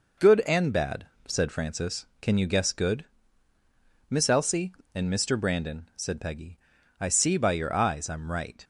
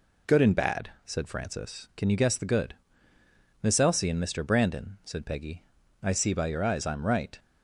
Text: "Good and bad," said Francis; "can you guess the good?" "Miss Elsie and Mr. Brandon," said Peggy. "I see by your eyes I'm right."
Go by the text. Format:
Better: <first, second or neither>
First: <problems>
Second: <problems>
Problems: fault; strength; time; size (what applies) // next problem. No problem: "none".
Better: second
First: skips "the"; at 2.7 s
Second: none